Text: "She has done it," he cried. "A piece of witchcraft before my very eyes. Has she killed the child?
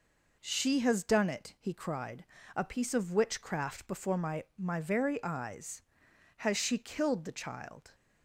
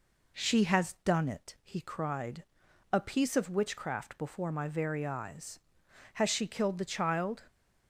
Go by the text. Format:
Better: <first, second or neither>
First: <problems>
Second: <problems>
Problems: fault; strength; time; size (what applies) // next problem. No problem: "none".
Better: second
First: says "my" twice; at 4.5 s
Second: none